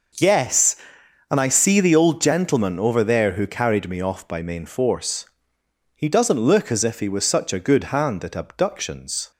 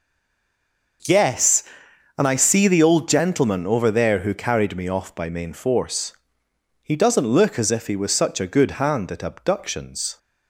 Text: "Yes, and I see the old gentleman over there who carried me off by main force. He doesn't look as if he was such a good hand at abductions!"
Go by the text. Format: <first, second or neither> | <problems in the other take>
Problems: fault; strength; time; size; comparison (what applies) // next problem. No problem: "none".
first | stays silent before the first word; until 1.0 s; 1.0 s long // starts louder than the rest; noticeable; until 2.6 s; 6 dB; noticeable in the first